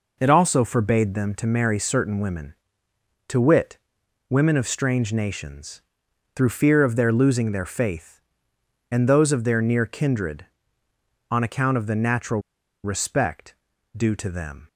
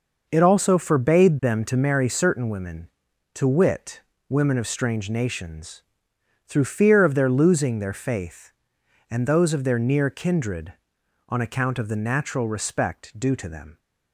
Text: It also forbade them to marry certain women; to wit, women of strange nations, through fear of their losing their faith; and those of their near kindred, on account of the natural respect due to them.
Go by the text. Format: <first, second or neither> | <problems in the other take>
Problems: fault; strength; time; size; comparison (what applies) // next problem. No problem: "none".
second | pauses between "natural" and "respect"; at 12.4 s; 0.42 s long // pauses between "respect" and "due"; at 13.5 s; 0.42 s long